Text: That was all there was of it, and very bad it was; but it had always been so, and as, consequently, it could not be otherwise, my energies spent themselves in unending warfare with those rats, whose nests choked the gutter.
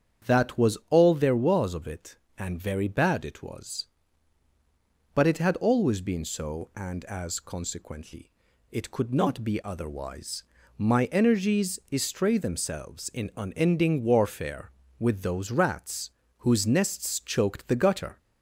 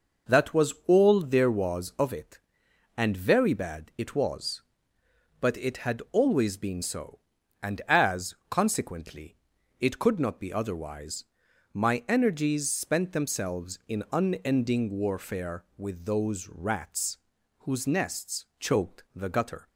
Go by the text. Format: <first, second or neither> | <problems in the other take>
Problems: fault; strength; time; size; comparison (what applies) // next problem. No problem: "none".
second | starts louder than the rest; strong; until 1.3 s; 8.5 dB // says "estray" for "spent"; at 11.9 s